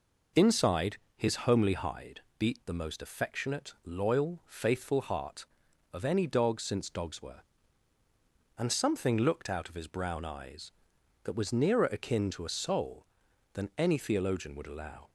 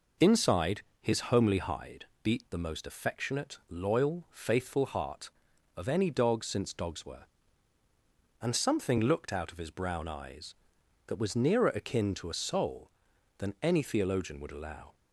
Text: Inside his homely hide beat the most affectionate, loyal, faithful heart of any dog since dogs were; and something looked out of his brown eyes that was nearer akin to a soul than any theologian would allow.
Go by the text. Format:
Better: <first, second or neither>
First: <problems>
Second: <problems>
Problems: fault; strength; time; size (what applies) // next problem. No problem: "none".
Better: neither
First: pauses between "Inside" and "his"; slight; at 0.9 s; 0.18 s long // pauses between "hide" and "beat"; slight; at 2.2 s; 0.18 s long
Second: pauses between "Inside" and "his"; slight; at 0.8 s; 0.18 s long // pauses between "hide" and "beat"; slight; at 2.0 s; 0.18 s long